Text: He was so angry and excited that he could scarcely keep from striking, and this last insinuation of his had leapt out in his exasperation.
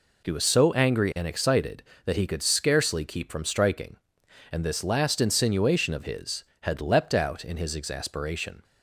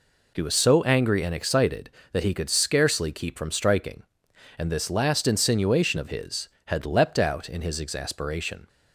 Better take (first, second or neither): neither